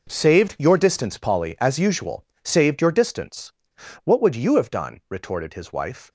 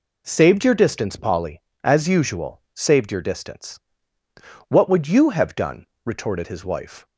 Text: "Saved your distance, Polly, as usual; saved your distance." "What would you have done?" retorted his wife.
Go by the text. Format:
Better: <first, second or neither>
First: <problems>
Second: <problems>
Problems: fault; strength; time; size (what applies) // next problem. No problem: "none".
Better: second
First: gets quieter; strong; throughout; 13.5 dB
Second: none